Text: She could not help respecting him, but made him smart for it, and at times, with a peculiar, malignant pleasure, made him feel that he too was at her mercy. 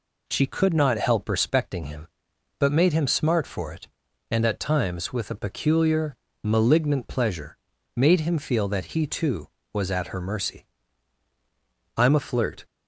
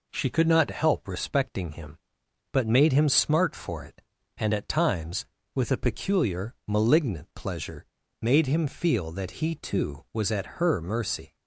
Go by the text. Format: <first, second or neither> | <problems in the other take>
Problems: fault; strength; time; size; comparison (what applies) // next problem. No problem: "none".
second | goes on to say "I'm a flirt"; noticeable; from 11.9 s on; 0.68 s long